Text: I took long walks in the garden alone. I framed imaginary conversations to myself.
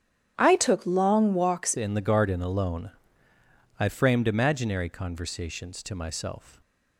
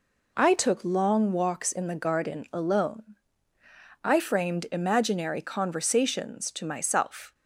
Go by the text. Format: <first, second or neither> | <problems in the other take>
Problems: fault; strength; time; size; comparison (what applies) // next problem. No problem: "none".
second | starts louder than the rest; strong; until 1.3 s; 9.5 dB // changes voice at "in"; from 1.7 s on; 4.9 s long